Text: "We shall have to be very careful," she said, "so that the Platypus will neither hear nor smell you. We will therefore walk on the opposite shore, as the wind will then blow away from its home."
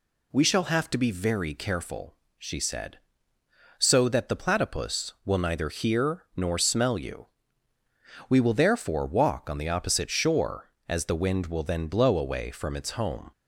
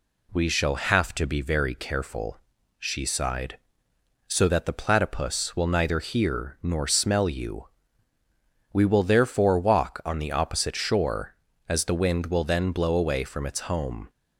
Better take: first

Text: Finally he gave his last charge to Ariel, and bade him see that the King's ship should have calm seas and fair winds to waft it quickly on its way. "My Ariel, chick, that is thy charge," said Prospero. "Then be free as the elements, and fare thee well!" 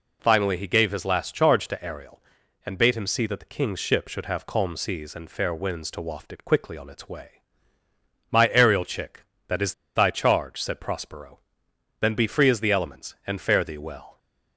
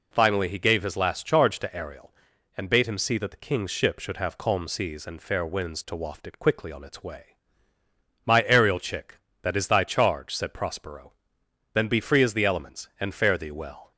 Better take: second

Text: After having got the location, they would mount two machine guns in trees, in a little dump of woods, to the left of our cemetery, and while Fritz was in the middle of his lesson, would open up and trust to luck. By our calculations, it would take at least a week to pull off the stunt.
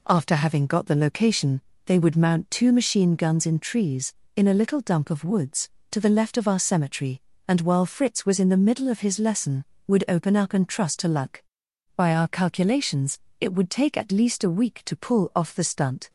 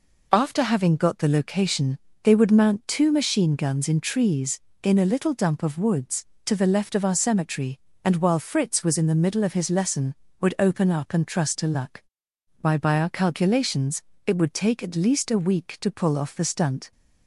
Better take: first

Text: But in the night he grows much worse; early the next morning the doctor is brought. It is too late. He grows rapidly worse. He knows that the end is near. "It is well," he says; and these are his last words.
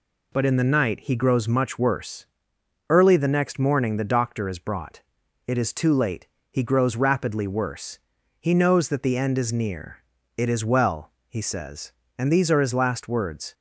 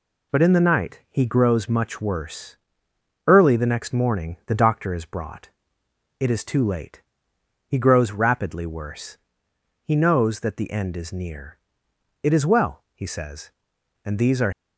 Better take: first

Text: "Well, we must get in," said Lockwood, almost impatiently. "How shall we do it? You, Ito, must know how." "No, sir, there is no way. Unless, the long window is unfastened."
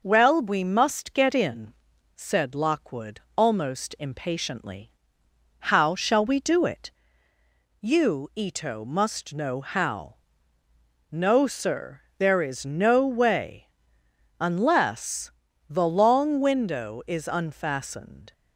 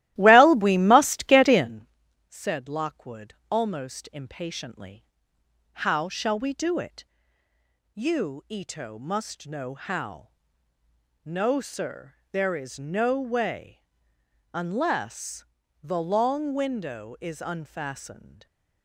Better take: first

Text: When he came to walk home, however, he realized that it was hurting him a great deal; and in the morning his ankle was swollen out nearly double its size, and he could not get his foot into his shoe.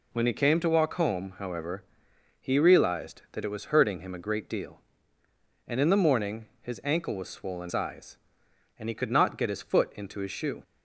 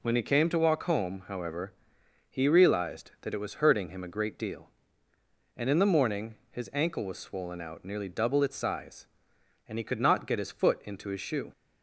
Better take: second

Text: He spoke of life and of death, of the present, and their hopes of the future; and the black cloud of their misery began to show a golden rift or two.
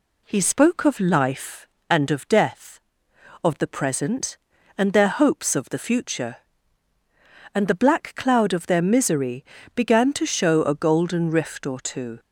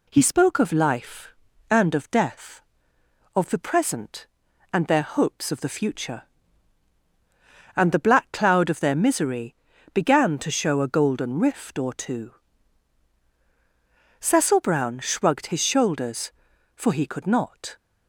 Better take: first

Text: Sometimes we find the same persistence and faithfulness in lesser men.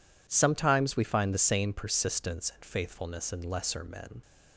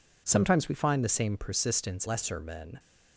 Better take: first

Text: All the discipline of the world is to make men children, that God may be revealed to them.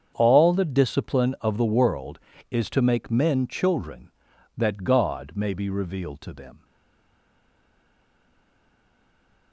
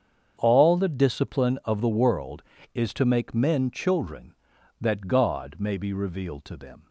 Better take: second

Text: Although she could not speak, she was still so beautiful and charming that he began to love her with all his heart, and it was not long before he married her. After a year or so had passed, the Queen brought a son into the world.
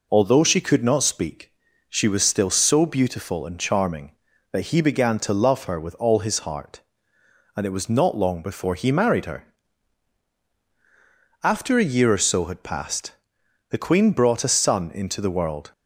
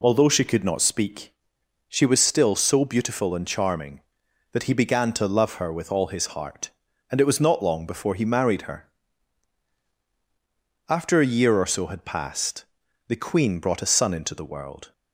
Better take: neither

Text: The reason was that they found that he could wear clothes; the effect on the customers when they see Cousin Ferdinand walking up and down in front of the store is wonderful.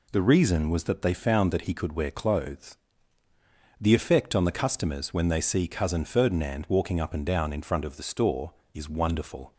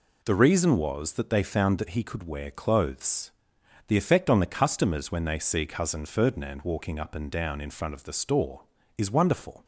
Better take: neither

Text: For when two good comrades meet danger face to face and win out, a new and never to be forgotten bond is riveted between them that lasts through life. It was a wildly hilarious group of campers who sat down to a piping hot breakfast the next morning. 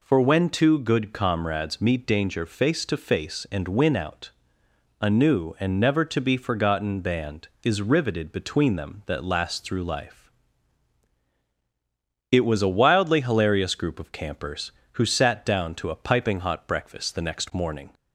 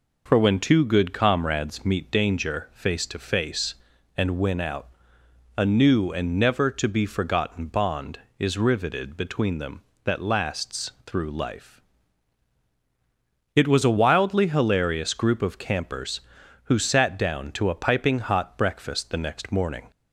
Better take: second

